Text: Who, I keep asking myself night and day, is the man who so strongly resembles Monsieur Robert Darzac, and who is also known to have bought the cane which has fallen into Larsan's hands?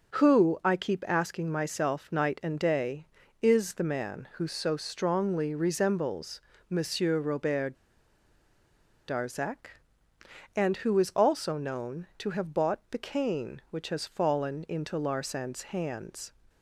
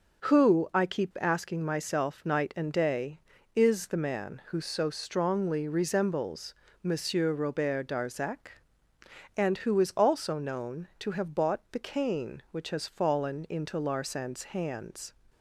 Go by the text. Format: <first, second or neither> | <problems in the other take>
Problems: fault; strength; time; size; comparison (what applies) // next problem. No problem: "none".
second | pauses between "resembles" and "Monsieur"; slight; at 6.4 s; 0.28 s long; slight in the second // pauses between "Robert" and "Darzac"; strong; at 7.7 s; 1.3 s long